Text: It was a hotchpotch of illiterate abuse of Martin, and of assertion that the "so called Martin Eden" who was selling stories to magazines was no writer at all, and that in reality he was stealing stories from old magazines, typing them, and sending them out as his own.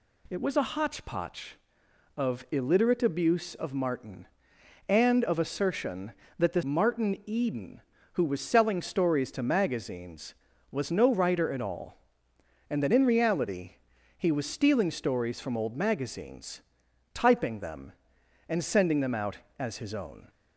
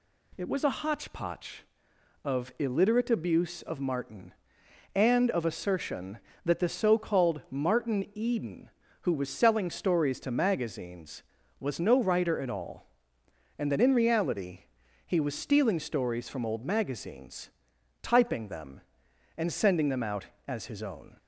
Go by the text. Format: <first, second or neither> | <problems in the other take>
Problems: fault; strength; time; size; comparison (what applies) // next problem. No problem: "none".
second | skips "so called"; at 6.6 s // pauses between "reality" and "he"; at 13.7 s; 0.44 s long; also in the second